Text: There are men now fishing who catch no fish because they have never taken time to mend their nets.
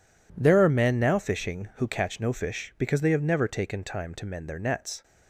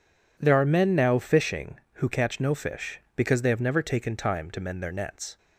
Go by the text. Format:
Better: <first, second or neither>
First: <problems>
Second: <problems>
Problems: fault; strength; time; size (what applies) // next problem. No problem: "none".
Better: neither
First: none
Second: none